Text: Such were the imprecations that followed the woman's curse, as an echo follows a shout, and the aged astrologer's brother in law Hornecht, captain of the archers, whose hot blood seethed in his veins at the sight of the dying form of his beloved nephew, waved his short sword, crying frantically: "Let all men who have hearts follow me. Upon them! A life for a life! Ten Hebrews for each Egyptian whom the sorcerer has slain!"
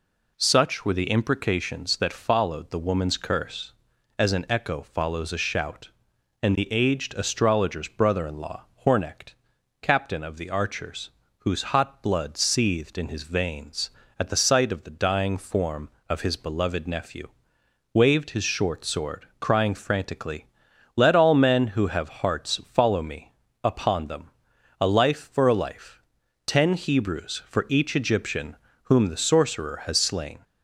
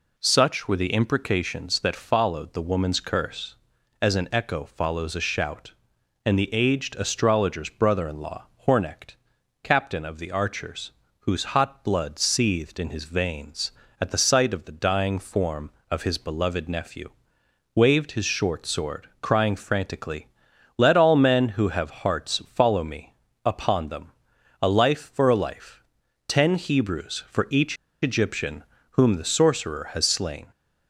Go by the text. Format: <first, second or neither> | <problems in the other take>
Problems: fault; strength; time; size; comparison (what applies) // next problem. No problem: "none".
first | pauses between "law" and "Hornecht"; slight; at 8.4 s; 0.20 s long; slight in the first // pauses between "each" and "Egyptian"; slight; at 27.7 s; 0.26 s long // pauses between "Egyptian" and "whom"; slight; at 28.6 s; 0.26 s long; slight in the first